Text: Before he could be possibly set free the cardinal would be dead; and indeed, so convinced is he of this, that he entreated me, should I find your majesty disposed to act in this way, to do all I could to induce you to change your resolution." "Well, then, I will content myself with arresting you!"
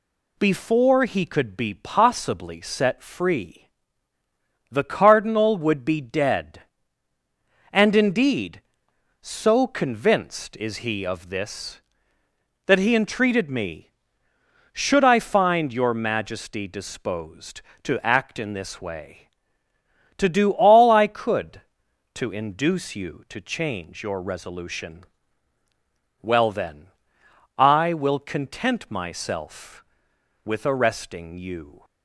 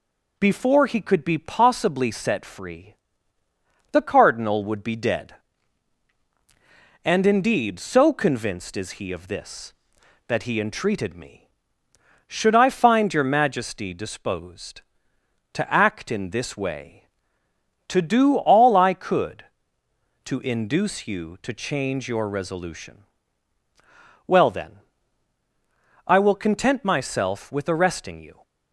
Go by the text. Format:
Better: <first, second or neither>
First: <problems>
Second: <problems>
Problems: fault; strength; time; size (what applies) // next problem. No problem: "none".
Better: neither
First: pauses between "free" and "the"; at 3.6 s; 1.0 s long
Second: pauses between "free" and "the"; noticeable; at 2.9 s; 0.98 s long